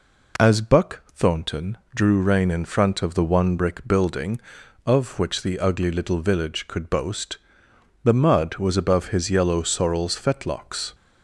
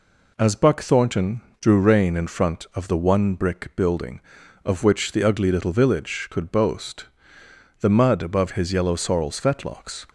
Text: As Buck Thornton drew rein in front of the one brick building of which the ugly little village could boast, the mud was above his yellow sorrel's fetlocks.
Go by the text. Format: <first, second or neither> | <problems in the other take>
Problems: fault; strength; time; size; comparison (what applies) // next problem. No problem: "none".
first | pauses between "Thornton" and "drew"; slight; at 1.4 s; 0.18 s long; slight in the first // skips "was"; at 8.2 s